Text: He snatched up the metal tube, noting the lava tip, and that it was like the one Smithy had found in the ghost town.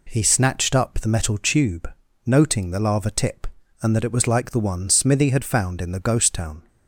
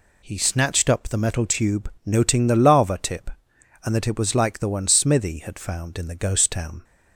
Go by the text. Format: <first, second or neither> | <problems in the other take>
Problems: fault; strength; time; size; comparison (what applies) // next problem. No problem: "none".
neither | none